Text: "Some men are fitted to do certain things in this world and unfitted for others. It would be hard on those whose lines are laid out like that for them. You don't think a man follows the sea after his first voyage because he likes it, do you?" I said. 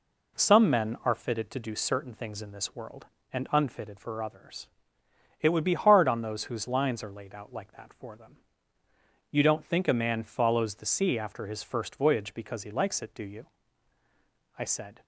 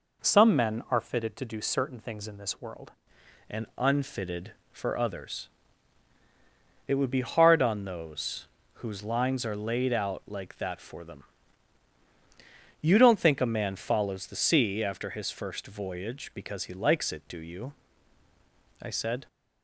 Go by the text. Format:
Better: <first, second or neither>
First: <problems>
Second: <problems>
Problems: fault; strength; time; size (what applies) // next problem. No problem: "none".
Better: first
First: none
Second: changes voice at "and"; from 3.4 s on; 15.8 s long // pauses between "those" and "whose"; slight; at 8.4 s; 0.36 s long